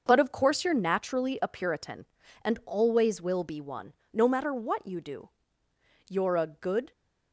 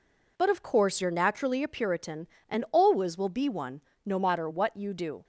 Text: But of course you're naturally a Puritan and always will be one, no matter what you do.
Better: second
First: starts louder than the rest; until 1.0 s; 6 dB // goes on to say "You're a good"; noticeable; from 6.0 s on; 0.84 s long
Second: none

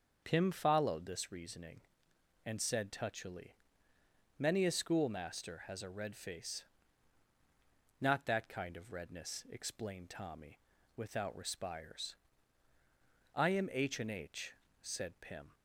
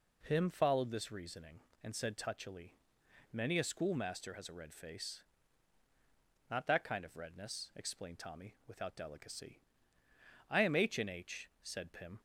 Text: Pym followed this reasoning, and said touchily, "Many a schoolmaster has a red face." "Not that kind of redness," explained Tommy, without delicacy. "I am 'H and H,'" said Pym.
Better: second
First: starts louder than the rest; until 1.2 s; 6.5 dB // says "respires" for "delicacy"; at 11.3 s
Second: none

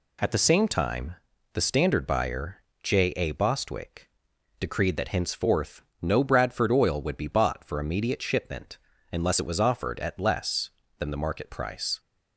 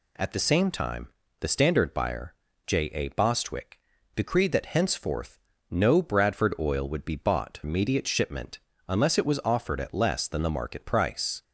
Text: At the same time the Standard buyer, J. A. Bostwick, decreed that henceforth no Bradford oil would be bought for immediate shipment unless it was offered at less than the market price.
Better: first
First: pauses between "time" and "the"; at 1.1 s; 0.38 s long // pauses between "henceforth" and "no"; slight; at 5.8 s; 0.20 s long // pauses between "shipment" and "unless"; slight; at 8.7 s; 0.36 s long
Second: pauses between "time" and "the"; slight; at 1.0 s; 0.32 s long // pauses between "henceforth" and "no"; slight; at 5.3 s; 0.32 s long // skips "for"; at 7.6 s // pauses between "shipment" and "unless"; slight; at 8.5 s; 0.30 s long

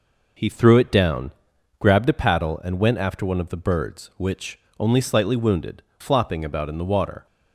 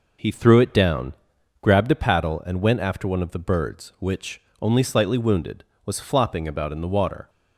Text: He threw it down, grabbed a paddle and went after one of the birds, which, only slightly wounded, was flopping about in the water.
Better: second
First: skips "was"; at 5.9 s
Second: none

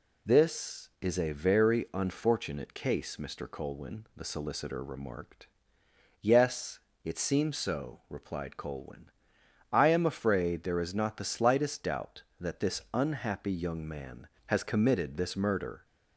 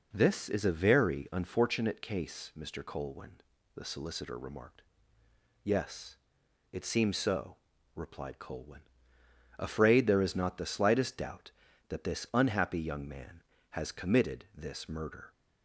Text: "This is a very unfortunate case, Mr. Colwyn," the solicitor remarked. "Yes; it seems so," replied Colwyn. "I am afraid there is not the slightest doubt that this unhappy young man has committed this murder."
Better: first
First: none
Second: skips "I am"; at 9.1 s

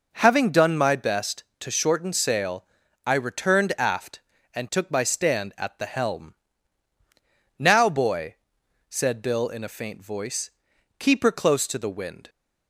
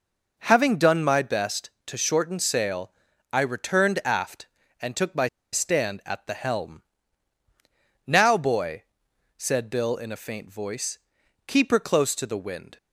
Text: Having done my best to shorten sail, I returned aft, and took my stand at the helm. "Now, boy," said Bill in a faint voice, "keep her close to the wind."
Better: first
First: none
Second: pauses between "my" and "stand"; slight; at 5.2 s; 0.25 s long

